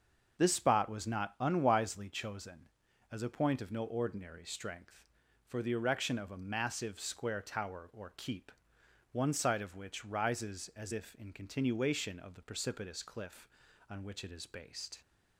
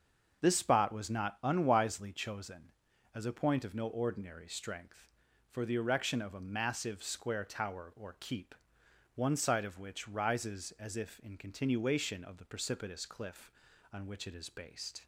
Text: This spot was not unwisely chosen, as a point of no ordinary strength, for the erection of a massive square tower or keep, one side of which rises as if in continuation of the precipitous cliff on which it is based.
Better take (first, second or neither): neither